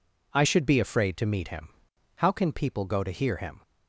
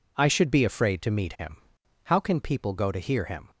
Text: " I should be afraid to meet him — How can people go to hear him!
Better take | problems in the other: neither | none

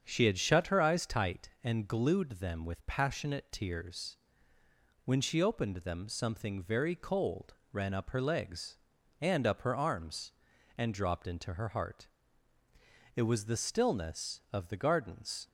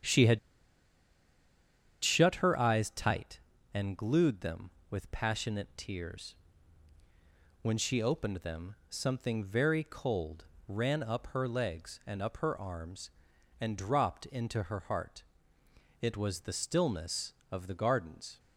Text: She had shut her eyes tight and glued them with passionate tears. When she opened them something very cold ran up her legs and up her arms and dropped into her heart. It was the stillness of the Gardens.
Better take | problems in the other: first | starts louder than the rest; strong; until 2.7 s; 8.5 dB; strong in the first // pauses between "had" and "shut"; strong; at 0.3 s; 1.6 s long // pauses between "cold" and "ran"; slight; at 10.4 s; 0.24 s long; slight in the first

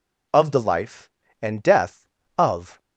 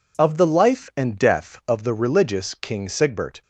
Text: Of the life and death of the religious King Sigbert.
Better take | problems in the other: second | stops before "the religious King Sigbert"; at 2.7 s

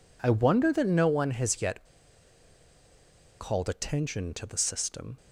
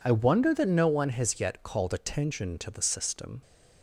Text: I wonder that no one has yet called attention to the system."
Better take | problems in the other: second | pauses between "yet" and "called"; strong; at 1.8 s; 1.5 s long

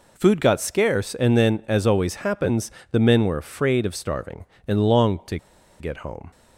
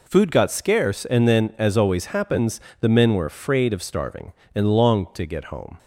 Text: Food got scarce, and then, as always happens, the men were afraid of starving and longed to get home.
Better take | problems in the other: second | pauses between "to" and "get"; at 5.3 s; 0.43 s long

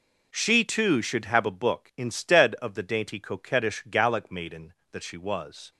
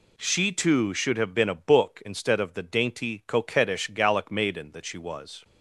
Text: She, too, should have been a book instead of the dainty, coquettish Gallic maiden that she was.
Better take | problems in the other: second | skips "been"; at 1.4 s

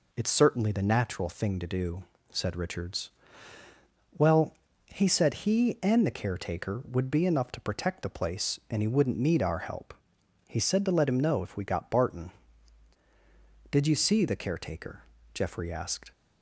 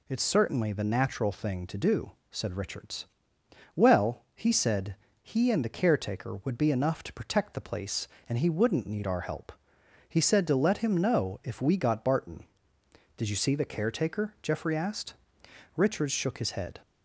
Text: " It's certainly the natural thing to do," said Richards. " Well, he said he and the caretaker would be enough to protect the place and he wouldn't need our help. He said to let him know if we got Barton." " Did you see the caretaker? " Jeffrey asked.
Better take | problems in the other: first | pauses between "said" and "he"; slight; at 4.9 s; 0.26 s long // goes on to say "Richards shook his head"; noticeable; from 15.7 s on; 1.0 s long

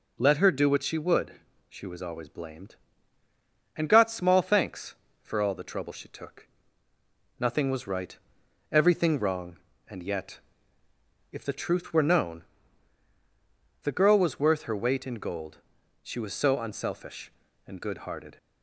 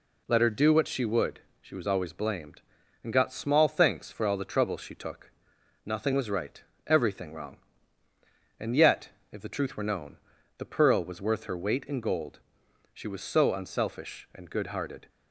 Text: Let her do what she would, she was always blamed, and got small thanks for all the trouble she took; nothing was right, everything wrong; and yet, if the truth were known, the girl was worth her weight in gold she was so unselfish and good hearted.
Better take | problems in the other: first | says "pearl" for "girl"; at 10.7 s // pauses between "gold" and "she"; noticeable; at 12.3 s; 0.56 s long; also in the first

